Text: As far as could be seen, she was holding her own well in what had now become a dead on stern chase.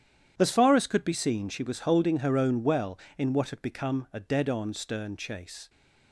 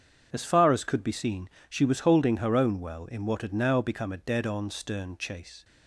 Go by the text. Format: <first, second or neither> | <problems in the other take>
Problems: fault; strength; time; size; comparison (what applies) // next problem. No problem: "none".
second | starts louder than the rest; strong; until 1.3 s; 9.5 dB; strong in the second // skips "now"; at 3.6 s